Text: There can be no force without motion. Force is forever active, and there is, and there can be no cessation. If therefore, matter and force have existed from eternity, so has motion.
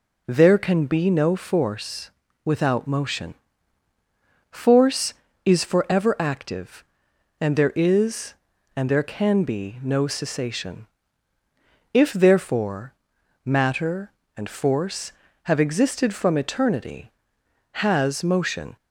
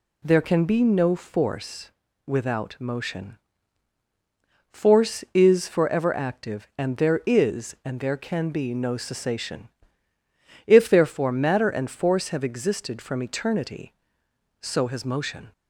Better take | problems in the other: second | pauses between "force" and "without"; slight; at 2.1 s; 0.34 s long; slight in the second // skips "so"; at 17.4 s

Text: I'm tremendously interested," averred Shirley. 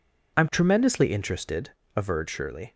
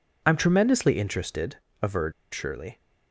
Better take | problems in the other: first | pauses between "averred" and "Shirley"; slight; at 2.1 s; 0.18 s long

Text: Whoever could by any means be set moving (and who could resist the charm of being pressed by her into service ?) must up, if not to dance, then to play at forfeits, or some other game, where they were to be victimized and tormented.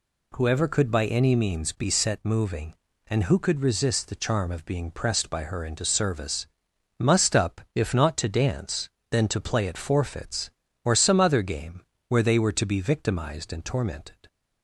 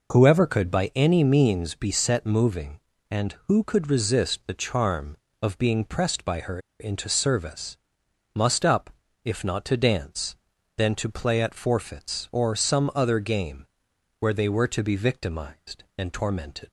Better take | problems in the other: first | pauses between "her" and "into"; slight; at 6.5 s; 0.20 s long

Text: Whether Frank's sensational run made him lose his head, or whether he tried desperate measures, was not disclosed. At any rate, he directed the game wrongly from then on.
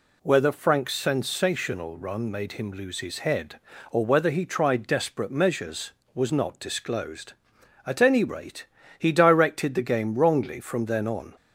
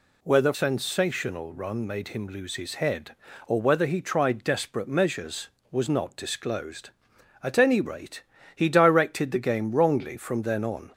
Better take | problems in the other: first | skips "Frank's"; at 0.5 s

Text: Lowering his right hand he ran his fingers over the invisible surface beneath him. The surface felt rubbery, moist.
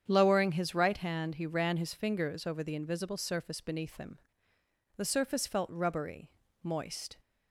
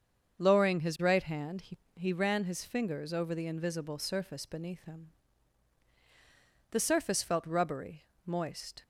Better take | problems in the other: first | starts louder than the rest; until 1.4 s; 7 dB; strong in the first // says "he" twice; at 1.9 s

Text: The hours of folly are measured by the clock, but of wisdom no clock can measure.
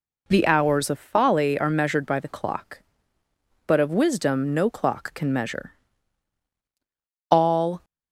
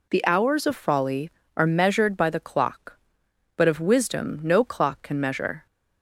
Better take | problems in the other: second | goes on to say "All"; from 7.3 s on; 0.54 s long

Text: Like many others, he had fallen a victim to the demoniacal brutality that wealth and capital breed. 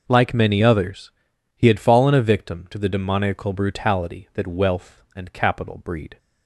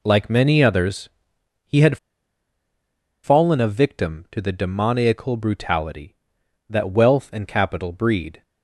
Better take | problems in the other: first | pauses between "had" and "fallen"; strong; at 1.9 s; 1.2 s long

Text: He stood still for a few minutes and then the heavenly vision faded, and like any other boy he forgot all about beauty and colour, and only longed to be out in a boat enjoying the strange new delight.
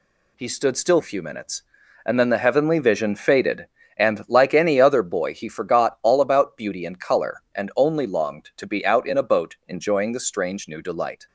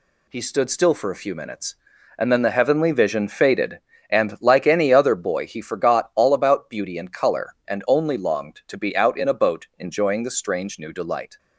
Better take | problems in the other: second | skips "for"; at 1.0 s

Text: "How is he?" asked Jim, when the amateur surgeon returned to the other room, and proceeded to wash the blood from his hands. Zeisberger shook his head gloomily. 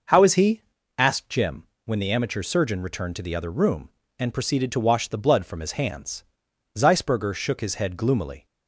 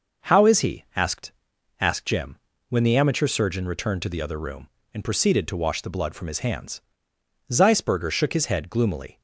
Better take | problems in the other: first | says "asked" twice; at 1.7 s

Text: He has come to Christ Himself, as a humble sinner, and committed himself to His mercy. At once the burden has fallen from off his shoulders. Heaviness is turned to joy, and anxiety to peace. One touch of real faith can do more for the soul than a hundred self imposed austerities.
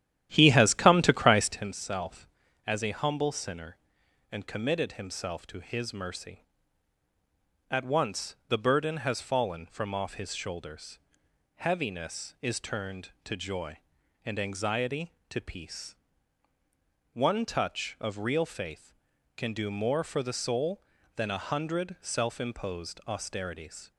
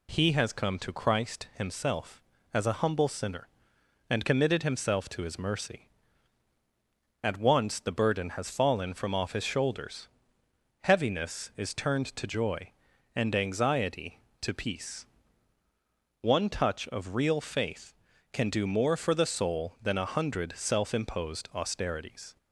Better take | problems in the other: second | starts louder than the rest; strong; until 1.7 s; 12 dB

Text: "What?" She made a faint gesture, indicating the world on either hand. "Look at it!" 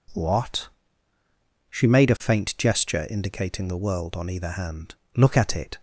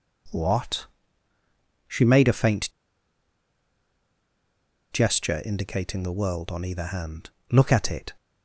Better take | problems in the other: first | pauses between "faint" and "gesture"; strong; at 2.7 s; 2.2 s long

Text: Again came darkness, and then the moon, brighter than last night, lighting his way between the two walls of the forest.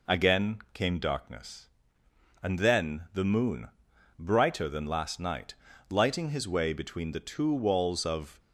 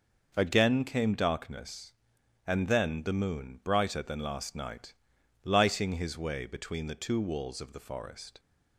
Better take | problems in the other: second | stops before "the forest"; at 8.3 s

